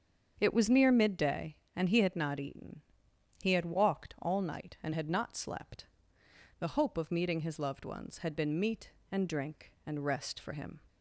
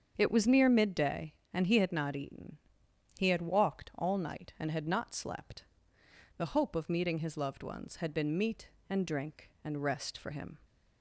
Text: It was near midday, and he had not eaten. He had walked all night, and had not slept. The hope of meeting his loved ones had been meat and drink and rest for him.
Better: neither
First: starts louder than the rest; strong; until 1.4 s; 7 dB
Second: starts louder than the rest; strong; until 1.1 s; 7 dB

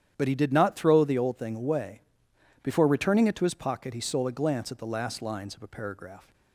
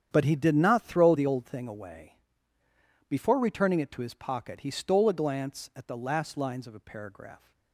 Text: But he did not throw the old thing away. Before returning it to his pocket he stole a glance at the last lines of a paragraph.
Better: neither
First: starts louder than the rest; strong; until 1.1 s; 9.5 dB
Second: starts louder than the rest; strong; until 1.1 s; 8.5 dB

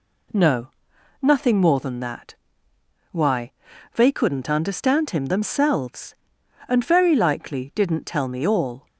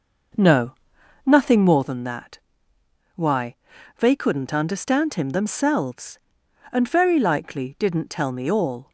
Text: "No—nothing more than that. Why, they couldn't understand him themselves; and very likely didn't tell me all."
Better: first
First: none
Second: starts louder than the rest; noticeable; until 1.9 s; 5.5 dB

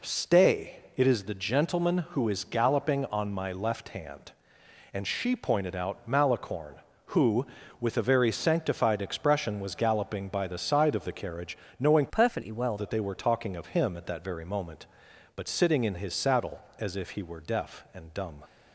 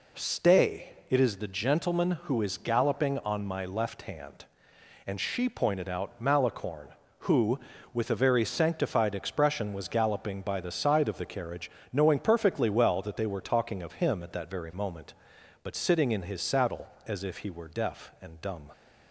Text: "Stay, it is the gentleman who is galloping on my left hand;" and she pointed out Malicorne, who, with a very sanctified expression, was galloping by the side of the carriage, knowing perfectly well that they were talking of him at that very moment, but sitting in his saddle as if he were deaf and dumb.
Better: second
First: changes voice from "perfectly" to "well"; from 12.0 to 12.7 s; 0.7 s long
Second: none

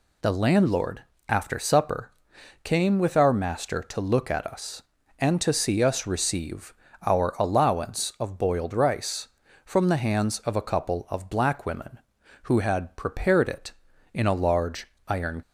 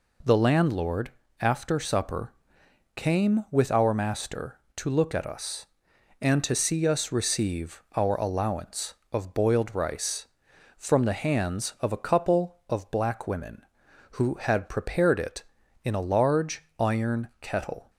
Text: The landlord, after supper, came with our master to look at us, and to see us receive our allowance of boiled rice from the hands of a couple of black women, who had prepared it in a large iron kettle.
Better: second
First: pauses between "receive" and "our"; slight; at 6.7 s; 0.32 s long // pauses between "large" and "iron"; slight; at 14.8 s; 0.22 s long // stops before "kettle"; at 15.4 s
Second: none

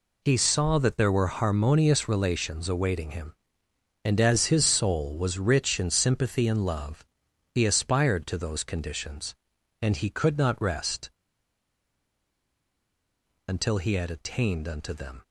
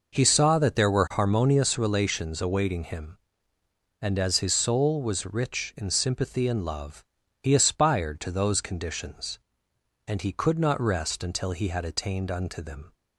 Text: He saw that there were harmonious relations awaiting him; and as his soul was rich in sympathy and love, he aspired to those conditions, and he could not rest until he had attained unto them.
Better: second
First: pauses between "rest" and "until"; strong; at 11.1 s; 2.3 s long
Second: none

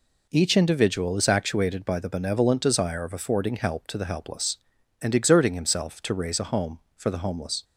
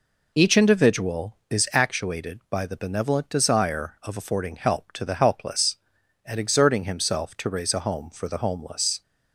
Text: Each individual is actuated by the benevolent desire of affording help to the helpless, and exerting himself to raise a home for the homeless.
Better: neither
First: none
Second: none

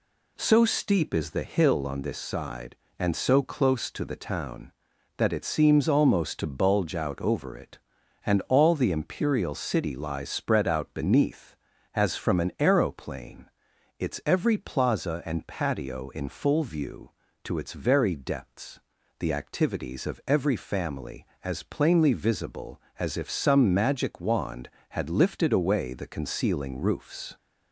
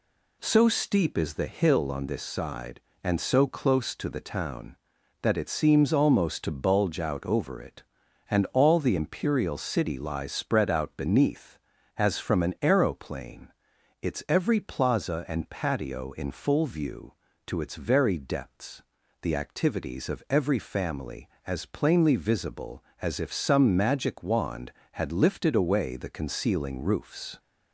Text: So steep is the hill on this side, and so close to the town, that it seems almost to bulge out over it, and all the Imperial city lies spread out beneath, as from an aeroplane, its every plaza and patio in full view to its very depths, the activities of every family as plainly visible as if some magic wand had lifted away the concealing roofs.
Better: neither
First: none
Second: none

